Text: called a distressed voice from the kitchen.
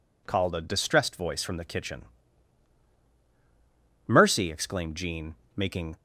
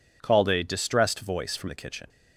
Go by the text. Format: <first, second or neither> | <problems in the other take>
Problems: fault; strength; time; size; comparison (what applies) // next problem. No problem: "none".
second | goes on to say "Mercy exclaimed Jean making"; strong; from 4.0 s on; 1.8 s long